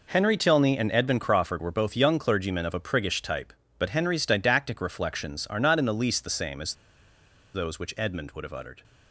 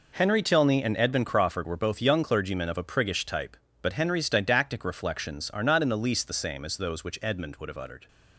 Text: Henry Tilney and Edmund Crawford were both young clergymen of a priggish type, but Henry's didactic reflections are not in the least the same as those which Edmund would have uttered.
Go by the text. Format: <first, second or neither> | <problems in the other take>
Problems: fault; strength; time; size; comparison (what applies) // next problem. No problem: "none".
second | pauses between "as" and "those"; noticeable; at 6.7 s; 0.81 s long